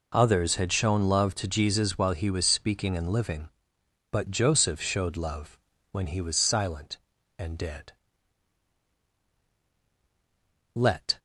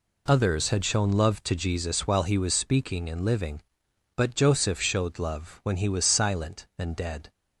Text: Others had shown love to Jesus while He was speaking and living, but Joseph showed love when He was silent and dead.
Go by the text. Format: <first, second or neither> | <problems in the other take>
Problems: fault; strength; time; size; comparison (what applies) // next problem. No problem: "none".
second | pauses between "love" and "when"; slight; at 5.5 s; 0.34 s long // goes on to say "Let"; slight; from 10.7 s on; 0.42 s long